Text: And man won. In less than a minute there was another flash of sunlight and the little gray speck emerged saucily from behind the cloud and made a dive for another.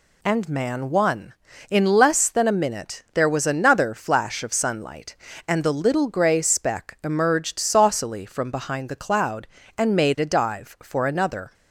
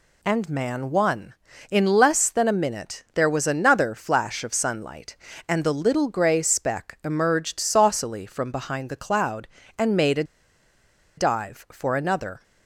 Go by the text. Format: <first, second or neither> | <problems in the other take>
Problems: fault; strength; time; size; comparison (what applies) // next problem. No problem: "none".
first | pauses between "a" and "dive"; noticeable; at 10.2 s; 0.93 s long